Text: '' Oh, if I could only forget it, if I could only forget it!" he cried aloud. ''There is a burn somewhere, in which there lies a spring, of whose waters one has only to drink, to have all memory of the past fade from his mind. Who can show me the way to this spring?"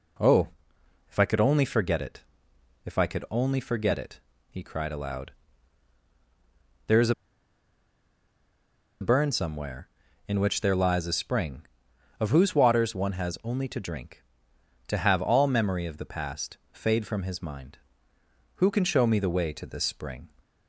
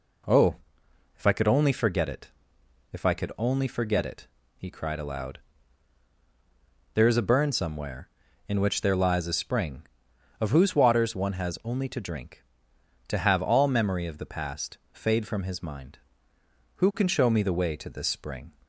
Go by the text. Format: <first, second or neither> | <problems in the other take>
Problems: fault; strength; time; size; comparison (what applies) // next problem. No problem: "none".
second | pauses between "is" and "a"; strong; at 7.1 s; 1.8 s long